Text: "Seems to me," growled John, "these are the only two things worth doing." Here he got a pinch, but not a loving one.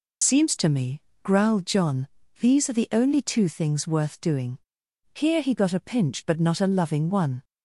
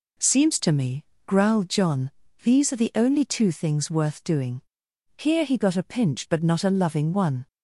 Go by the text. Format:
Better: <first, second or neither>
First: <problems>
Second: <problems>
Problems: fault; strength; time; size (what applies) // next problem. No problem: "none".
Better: second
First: loses the start of "Seems"; at 0.2 s; 60 ms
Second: none